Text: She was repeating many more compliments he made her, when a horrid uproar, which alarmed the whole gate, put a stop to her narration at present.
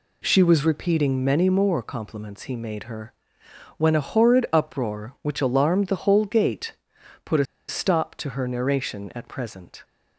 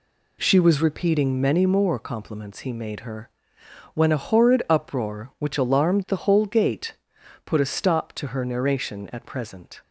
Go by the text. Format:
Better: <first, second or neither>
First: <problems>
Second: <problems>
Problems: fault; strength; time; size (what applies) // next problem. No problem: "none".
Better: second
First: pauses between "a" and "stop"; slight; at 7.4 s; 0.23 s long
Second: none